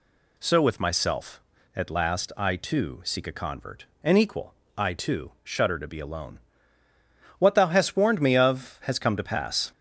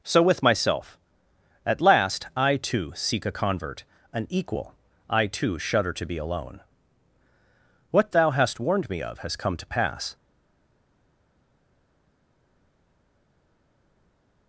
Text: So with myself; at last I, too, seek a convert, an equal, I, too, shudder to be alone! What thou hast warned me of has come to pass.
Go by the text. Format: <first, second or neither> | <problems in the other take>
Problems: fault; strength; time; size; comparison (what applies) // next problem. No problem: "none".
first | stays silent after the last word; strong; from 10.1 s on; 4.3 s long